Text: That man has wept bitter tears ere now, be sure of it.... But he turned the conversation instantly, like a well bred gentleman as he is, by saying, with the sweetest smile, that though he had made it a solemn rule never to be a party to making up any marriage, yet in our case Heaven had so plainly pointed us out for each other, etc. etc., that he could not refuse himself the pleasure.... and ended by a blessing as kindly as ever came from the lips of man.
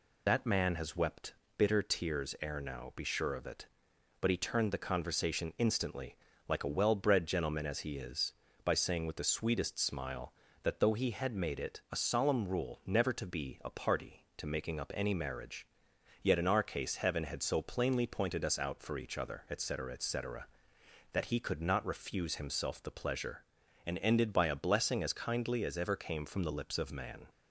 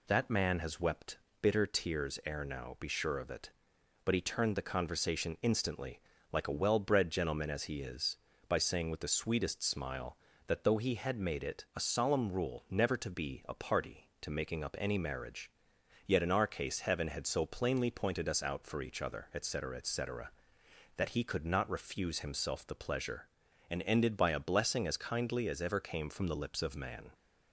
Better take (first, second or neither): second